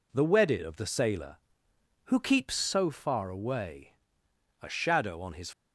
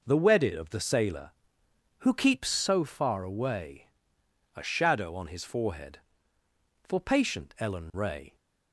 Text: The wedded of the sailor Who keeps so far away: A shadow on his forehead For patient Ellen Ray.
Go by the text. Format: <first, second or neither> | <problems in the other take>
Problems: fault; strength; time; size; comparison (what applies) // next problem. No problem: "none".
second | stops before "forehead For patient Ellen Ray"; at 5.5 s